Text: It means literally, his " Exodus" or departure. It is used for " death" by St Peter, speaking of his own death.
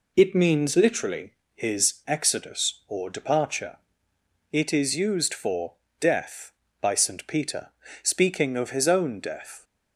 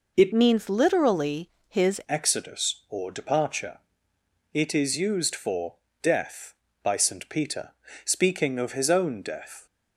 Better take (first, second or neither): first